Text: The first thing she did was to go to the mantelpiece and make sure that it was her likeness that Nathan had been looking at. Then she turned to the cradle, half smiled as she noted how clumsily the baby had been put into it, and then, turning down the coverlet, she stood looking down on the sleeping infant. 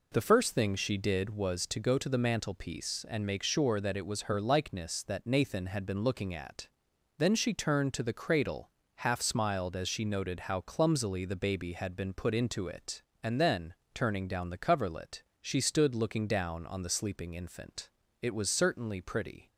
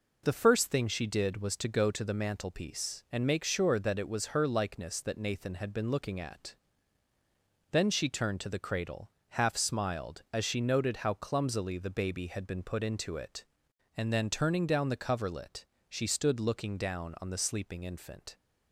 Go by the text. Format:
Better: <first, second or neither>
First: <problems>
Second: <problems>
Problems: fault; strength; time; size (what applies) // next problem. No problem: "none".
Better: second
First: goes on to say "It was certainly pretty"; noticeable; from 18.2 s on; 1.2 s long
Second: none